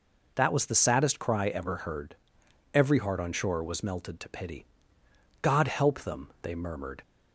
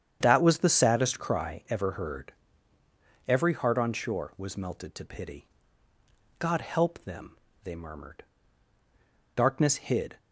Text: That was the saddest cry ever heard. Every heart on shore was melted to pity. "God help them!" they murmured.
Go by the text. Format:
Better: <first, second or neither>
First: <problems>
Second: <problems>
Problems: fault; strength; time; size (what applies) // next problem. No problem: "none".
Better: first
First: none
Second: starts louder than the rest; strong; until 1.2 s; 8.5 dB // goes on to say "Darkness hid"; noticeable; from 9.3 s on; 0.84 s long